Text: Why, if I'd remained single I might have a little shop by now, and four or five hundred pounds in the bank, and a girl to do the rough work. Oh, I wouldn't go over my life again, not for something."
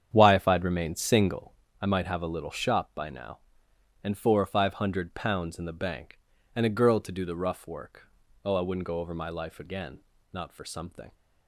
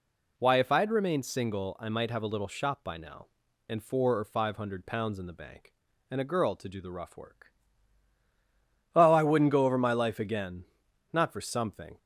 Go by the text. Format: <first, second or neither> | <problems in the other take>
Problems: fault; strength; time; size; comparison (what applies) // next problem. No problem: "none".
second | starts louder than the rest; strong; until 1.8 s; 8.5 dB // pauses between "single" and "I"; slight; at 1.5 s; 0.28 s long